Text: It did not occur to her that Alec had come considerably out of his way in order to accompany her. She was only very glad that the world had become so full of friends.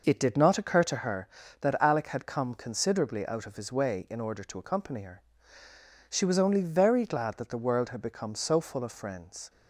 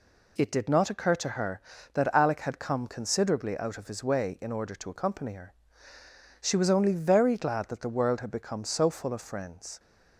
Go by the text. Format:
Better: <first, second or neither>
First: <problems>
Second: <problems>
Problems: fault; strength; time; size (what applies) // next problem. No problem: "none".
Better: second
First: starts louder than the rest; noticeable; until 1.1 s; 5.5 dB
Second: none